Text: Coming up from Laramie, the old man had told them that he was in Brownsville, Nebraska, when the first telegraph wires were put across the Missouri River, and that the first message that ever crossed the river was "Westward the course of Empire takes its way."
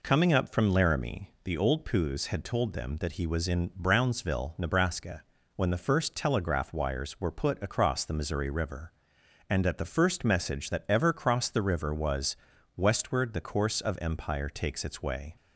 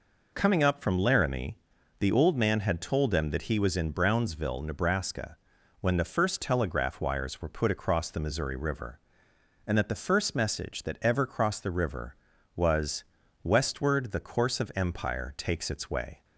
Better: second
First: says "poos" for "man"; at 1.8 s // pauses between "was" and "Westward"; at 12.3 s; 0.40 s long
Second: pauses between "was" and "Westward"; at 13.0 s; 0.40 s long

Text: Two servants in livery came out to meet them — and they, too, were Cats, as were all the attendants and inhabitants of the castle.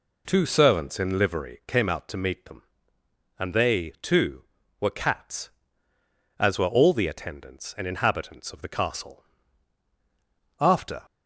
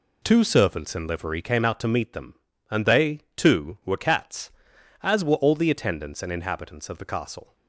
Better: second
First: goes on to say "After"; slight; from 10.6 s on; 0.42 s long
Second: none

